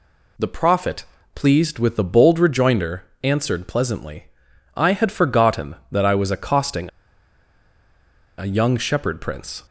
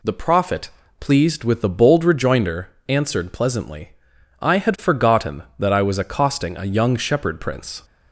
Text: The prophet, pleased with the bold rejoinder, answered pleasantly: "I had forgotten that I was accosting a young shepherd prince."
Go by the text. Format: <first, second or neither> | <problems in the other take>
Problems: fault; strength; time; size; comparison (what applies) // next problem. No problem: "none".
second | pauses between "accosting" and "a"; strong; at 6.8 s; 1.4 s long